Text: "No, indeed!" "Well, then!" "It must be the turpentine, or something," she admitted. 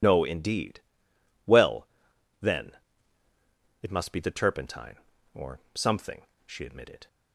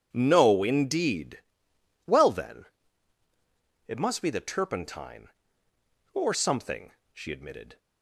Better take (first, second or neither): second